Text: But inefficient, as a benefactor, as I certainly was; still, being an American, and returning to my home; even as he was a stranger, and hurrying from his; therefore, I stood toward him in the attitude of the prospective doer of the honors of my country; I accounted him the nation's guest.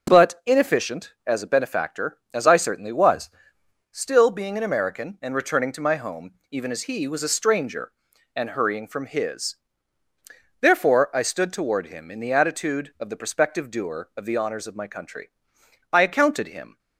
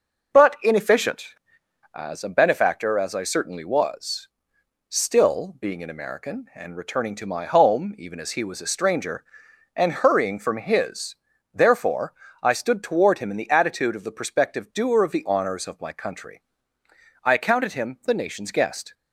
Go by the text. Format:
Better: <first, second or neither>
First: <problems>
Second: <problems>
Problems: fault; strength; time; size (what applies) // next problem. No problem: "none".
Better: second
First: stops before "the nation's guest"; at 16.7 s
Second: none